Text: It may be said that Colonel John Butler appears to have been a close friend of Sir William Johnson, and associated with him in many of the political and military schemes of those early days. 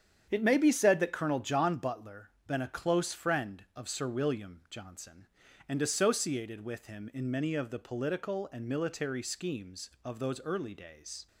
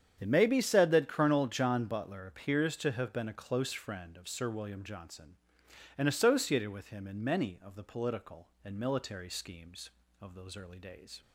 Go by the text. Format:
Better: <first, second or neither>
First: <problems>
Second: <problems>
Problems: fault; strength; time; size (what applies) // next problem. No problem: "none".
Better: second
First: starts louder than the rest; strong; until 1.3 s; 8 dB // skips "appears to have"; at 2.3 s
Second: starts louder than the rest; strong; until 1.1 s; 8 dB